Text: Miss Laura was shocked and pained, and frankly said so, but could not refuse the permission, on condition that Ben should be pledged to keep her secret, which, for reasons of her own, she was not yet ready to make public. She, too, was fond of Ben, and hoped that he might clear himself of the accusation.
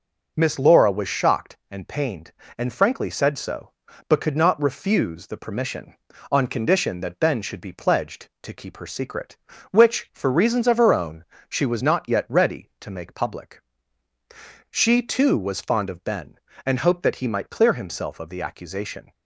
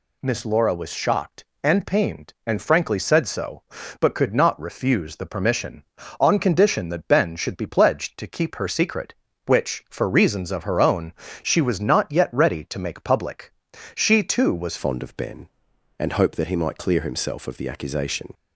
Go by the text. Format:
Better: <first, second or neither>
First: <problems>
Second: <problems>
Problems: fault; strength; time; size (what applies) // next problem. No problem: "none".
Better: first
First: none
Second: changes voice at "fond"; from 14.7 s on; 3.6 s long